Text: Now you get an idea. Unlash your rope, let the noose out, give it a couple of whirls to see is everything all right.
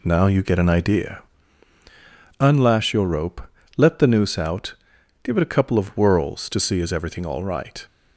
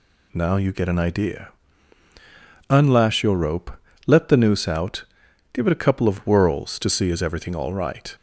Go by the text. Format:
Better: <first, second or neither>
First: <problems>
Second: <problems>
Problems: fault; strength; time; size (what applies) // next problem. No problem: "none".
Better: second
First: starts louder than the rest; slight; until 1.4 s; 2 dB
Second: none